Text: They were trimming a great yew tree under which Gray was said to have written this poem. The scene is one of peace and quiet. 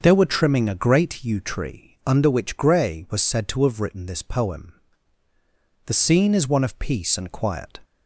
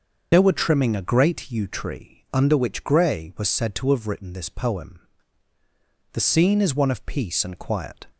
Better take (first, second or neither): first